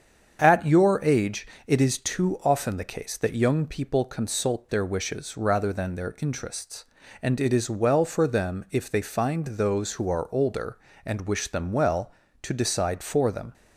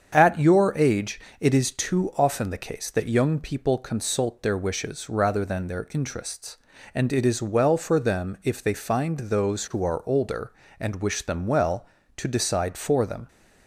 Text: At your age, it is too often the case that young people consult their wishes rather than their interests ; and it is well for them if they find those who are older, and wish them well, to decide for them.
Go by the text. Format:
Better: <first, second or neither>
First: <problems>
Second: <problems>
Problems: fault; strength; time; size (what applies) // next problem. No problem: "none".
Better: neither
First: starts louder than the rest; strong; until 1.4 s; 7.5 dB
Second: starts louder than the rest; strong; until 1.1 s; 7.5 dB